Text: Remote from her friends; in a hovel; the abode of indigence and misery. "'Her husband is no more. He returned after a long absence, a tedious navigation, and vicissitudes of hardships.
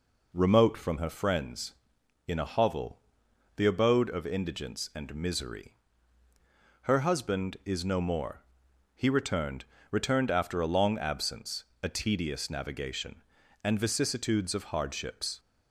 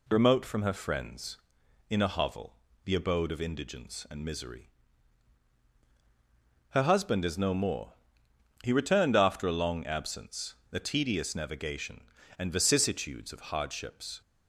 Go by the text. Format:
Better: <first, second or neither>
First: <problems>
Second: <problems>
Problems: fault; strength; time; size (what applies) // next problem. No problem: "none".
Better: second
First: says "returned" twice; at 9.8 s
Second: none